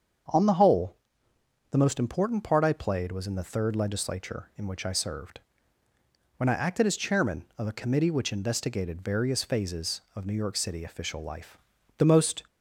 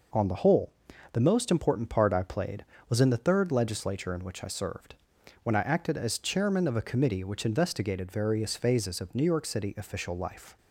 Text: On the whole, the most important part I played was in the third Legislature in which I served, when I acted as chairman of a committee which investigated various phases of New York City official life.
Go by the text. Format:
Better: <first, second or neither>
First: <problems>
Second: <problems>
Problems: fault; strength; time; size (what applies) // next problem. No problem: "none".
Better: second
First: starts louder than the rest; strong; until 2.0 s; 7.5 dB // goes on to say "The most"; slight; from 11.9 s on; 0.46 s long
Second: none